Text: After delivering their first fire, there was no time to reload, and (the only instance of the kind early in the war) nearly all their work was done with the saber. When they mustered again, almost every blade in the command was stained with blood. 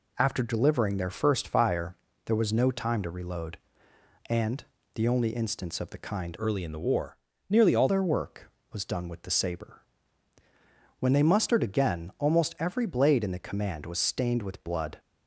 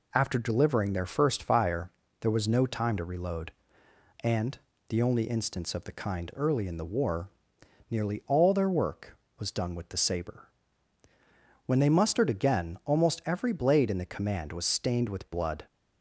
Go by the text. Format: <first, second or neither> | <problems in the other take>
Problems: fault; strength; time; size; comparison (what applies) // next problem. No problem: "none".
second | changes voice from "early" to "all"; from 6.3 to 7.8 s; 1.5 s long